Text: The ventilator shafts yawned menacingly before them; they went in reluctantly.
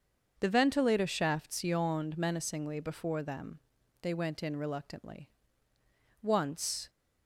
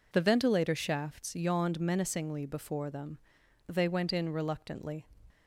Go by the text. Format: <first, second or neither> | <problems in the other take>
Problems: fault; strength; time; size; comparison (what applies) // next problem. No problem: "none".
second | starts louder than the rest; until 1.4 s; 6.5 dB // goes on to say "Once"; noticeable; from 6.2 s on; 0.68 s long